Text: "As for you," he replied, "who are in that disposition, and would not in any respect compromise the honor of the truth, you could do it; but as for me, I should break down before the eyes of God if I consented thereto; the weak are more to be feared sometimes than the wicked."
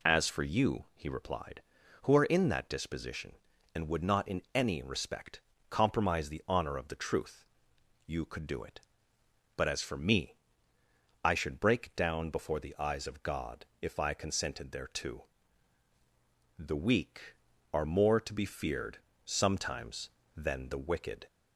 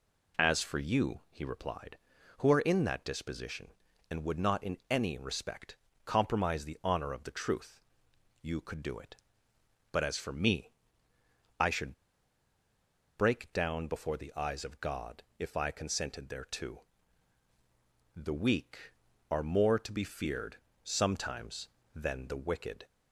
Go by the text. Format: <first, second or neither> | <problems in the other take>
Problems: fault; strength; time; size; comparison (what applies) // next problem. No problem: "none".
first | pauses between "respect" and "compromise"; slight; at 5.7 s; 0.26 s long; slight in the first // pauses between "should" and "break"; at 11.9 s; 1.2 s long // pauses between "God" and "if"; slight; at 15.2 s; 0.16 s long; slight in the first // pauses between "feared" and "sometimes"; slight; at 20.5 s; 0.26 s long; slight in the first